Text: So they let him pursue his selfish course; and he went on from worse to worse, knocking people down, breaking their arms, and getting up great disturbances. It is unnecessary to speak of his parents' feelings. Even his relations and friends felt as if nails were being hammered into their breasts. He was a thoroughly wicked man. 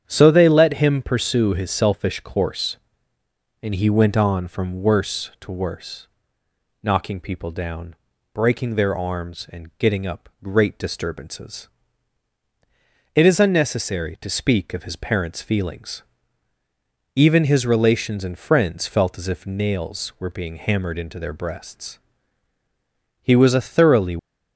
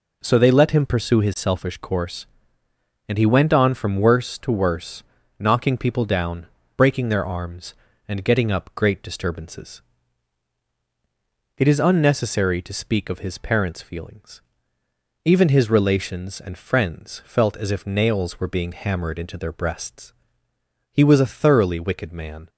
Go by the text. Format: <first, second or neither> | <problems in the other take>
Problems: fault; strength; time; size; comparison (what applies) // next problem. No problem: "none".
second | starts louder than the rest; strong; until 1.0 s; 9 dB // stops before "wicked man"; at 24.1 s